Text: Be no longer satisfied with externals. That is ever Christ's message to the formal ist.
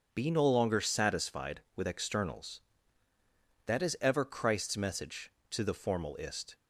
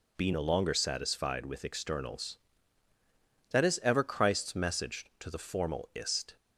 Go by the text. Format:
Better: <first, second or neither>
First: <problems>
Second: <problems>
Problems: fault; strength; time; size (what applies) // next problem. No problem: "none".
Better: neither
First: none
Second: none